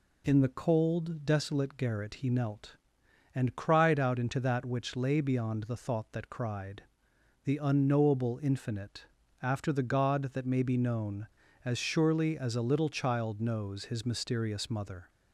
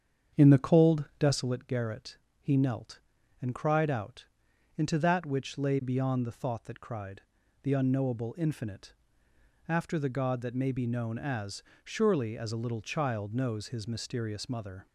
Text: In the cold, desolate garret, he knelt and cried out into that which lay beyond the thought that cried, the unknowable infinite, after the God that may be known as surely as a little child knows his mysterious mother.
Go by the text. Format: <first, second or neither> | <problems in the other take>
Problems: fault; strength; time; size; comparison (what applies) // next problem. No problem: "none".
first | starts louder than the rest; strong; until 1.6 s; 8 dB // pauses between "out" and "into"; noticeable; at 4.2 s; 0.54 s long // pauses between "as" and "surely"; slight; at 11.6 s; 0.22 s long